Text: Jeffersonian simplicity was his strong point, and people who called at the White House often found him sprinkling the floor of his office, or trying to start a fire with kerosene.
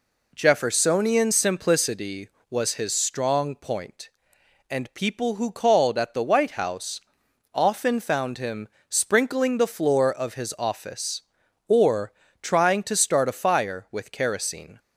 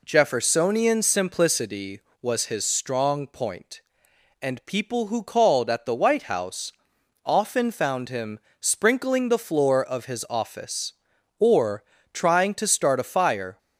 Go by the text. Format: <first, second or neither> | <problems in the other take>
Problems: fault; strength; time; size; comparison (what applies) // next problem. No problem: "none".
first | pauses between "House" and "often"; noticeable; at 6.7 s; 0.53 s long; noticeable in the first // pauses between "him" and "sprinkling"; slight; at 8.3 s; 0.20 s long; slight in the first // pauses between "or" and "trying"; slight; at 11.8 s; 0.28 s long; slight in the first // stops before "with kerosene"; at 13.5 s